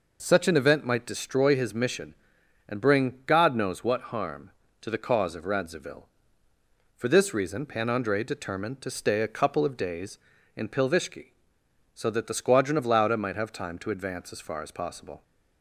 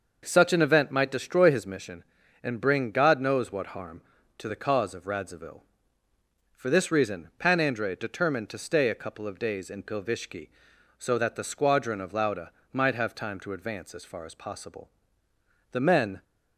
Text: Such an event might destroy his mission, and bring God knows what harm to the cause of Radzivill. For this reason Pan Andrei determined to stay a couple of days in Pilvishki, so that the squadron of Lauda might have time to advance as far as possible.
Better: first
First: none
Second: starts louder than the rest; noticeable; until 1.2 s; 6 dB // pauses between "Lauda" and "might"; slight; at 12.5 s; 0.20 s long // goes on to say "The men"; from 15.7 s on; 0.50 s long

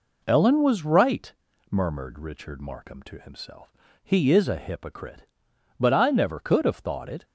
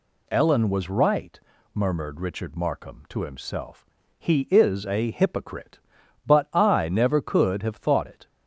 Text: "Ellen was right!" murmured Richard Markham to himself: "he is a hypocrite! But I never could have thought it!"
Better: neither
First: none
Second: none

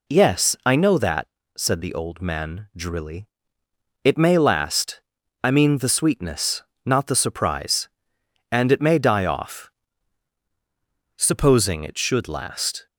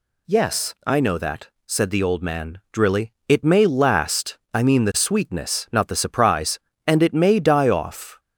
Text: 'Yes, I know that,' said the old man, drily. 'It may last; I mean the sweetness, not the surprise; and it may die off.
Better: second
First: goes on to say "Supposing it should last"; strong; from 11.1 s on; 1.7 s long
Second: none

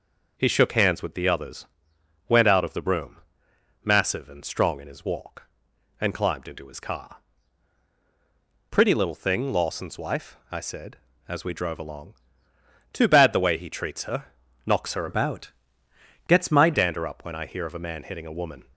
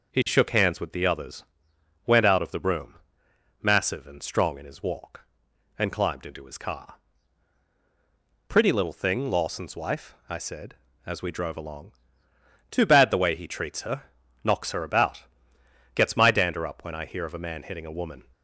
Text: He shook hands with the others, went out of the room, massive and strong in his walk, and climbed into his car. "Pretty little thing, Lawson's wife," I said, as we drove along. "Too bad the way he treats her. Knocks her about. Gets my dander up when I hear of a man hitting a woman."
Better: second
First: starts louder than the rest; noticeable; until 1.3 s; 6 dB // changes voice from "about" to "my"; from 15.0 to 16.7 s; 1.7 s long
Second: starts louder than the rest; noticeable; until 1.1 s; 6 dB

